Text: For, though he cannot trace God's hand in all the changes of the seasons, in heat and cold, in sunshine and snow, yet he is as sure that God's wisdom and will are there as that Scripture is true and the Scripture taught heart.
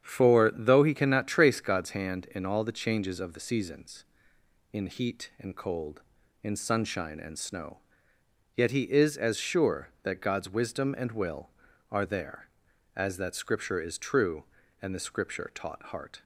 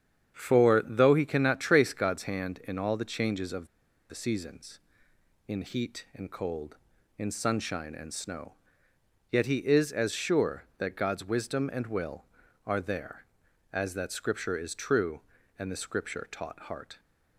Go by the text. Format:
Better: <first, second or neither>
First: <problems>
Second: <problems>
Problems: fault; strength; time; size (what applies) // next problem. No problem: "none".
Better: first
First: starts louder than the rest; strong; until 1.0 s; 8.5 dB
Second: starts louder than the rest; strong; until 1.3 s; 8.5 dB // pauses between "of" and "the"; at 3.6 s; 0.44 s long